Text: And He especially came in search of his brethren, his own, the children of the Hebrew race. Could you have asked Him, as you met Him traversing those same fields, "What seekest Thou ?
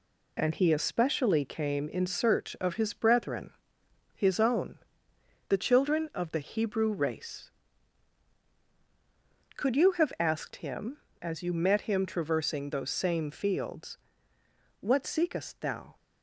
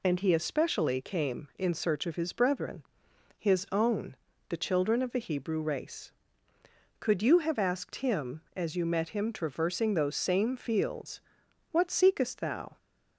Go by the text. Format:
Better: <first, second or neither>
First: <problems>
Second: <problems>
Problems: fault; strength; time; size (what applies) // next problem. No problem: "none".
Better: second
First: gets quieter; noticeable; throughout; 5.5 dB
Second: none